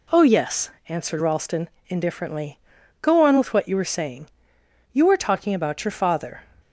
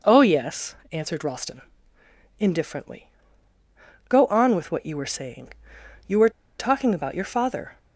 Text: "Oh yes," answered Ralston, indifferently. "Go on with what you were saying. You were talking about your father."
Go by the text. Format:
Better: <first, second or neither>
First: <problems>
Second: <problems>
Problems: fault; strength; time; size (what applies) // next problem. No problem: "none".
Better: first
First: none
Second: pauses between "were" and "talking"; slight; at 6.3 s; 0.28 s long